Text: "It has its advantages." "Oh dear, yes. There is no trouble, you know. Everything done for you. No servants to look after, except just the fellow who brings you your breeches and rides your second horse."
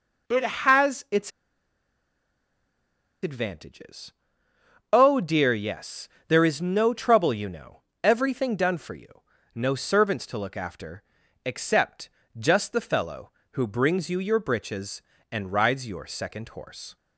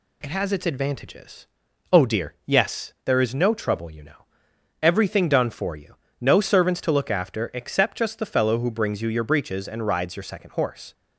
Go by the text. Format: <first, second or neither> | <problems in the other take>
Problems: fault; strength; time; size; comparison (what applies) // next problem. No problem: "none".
second | pauses between "its" and "advantages"; strong; at 1.2 s; 1.9 s long // pauses between "except" and "just"; slight; at 12.0 s; 0.28 s long